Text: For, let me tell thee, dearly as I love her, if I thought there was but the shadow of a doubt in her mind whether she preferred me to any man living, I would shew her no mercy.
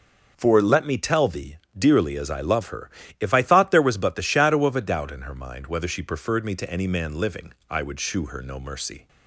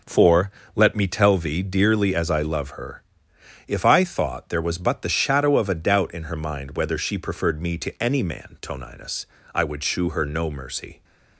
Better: first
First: none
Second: says "toninus" for "living"; at 8.6 s

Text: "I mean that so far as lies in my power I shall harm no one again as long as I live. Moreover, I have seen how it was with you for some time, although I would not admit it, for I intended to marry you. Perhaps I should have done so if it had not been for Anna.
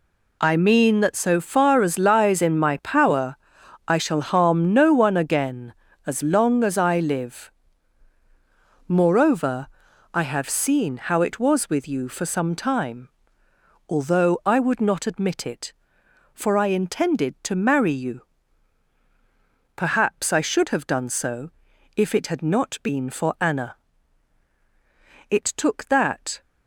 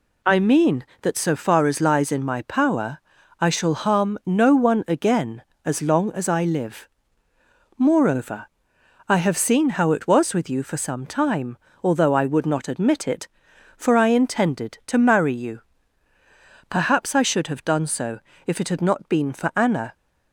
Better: second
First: pauses between "power" and "I"; noticeable; at 3.3 s; 0.50 s long // pauses between "so" and "if"; noticeable; at 21.5 s; 0.46 s long // goes on to say "It took that"; noticeable; from 25.3 s on; 1.1 s long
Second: pauses between "power" and "I"; at 2.9 s; 0.42 s long // pauses between "so" and "if"; slight; at 18.2 s; 0.26 s long

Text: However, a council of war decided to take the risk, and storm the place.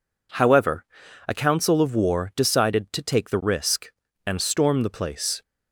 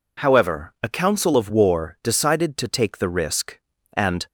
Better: first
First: none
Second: stops before "storm the place"; at 4.2 s

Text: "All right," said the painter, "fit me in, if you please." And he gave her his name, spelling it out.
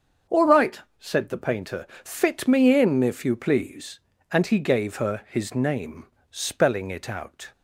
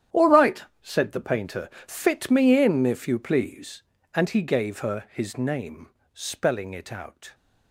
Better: first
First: starts louder than the rest; until 1.4 s; 7 dB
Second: gets quieter; strong; throughout; 15 dB // starts louder than the rest; strong; until 1.3 s; 10.5 dB

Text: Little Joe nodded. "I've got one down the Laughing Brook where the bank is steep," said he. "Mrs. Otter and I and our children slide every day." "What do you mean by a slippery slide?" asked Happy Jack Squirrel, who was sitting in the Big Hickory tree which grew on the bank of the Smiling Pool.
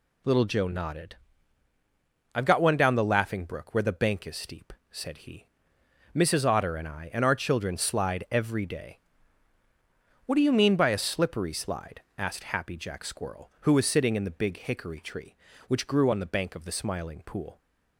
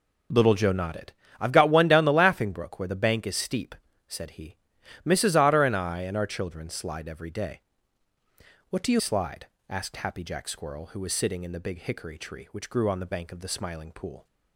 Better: first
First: none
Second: skips "mean by a slippery"; at 8.9 s

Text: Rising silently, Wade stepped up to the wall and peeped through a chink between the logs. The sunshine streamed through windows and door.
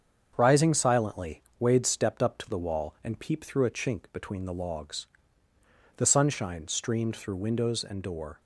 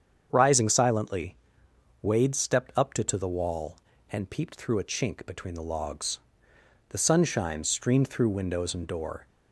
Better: first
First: starts louder than the rest; strong; until 1.3 s; 7.5 dB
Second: starts louder than the rest; strong; until 1.3 s; 7.5 dB // says "to" twice; at 3.0 s

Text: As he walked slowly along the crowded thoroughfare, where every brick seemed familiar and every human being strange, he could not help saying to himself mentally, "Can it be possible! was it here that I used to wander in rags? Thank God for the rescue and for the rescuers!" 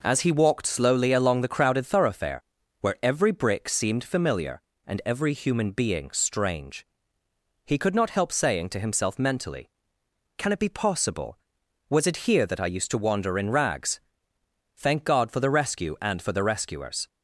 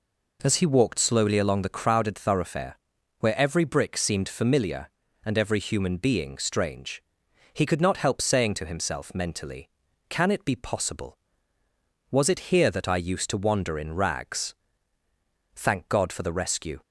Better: first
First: none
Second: stops before "and for the rescuers"; at 16.8 s

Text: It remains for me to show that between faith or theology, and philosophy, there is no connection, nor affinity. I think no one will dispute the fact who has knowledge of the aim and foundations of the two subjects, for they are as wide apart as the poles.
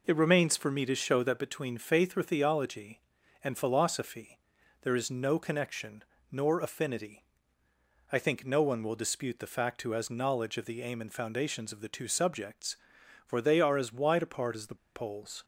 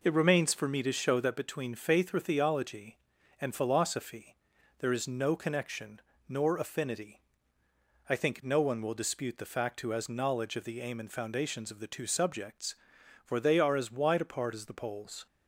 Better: second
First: pauses between "the" and "poles"; slight; at 14.7 s; 0.19 s long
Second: none

